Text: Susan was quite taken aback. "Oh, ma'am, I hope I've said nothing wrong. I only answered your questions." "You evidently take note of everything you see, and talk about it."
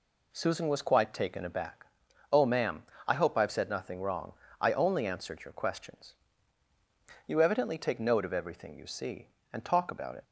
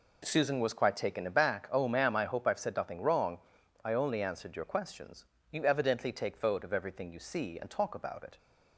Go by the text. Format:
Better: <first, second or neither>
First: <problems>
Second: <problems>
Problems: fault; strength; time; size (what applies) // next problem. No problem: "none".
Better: first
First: none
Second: says "vote" for "note"; at 6.3 s